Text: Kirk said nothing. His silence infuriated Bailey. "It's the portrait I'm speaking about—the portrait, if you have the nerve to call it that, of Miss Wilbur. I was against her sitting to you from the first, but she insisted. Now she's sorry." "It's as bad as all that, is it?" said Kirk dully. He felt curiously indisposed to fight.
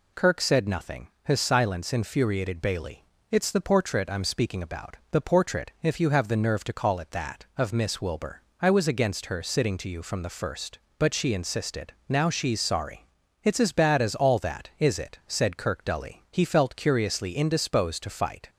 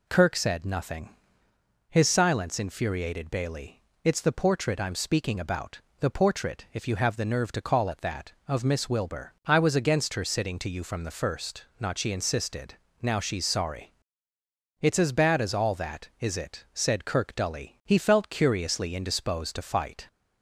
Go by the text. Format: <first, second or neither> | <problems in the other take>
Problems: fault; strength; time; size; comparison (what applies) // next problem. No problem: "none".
first | says "not" for "but"; at 11.7 s